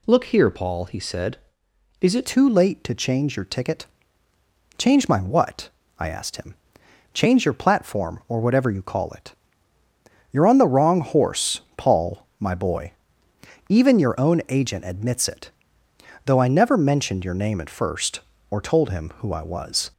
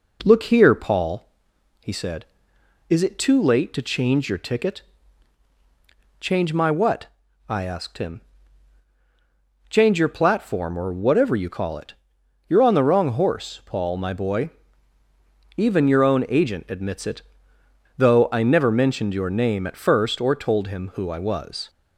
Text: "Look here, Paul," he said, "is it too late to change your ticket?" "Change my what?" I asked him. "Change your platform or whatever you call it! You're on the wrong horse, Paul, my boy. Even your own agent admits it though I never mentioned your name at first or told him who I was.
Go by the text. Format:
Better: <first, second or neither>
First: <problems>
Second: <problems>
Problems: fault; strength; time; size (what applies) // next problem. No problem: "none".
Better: second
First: changes voice at "too"; from 2.2 s on; 17.7 s long // pauses between "it" and "though"; noticeable; at 15.4 s; 0.76 s long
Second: pauses between "it" and "though"; noticeable; at 17.2 s; 0.74 s long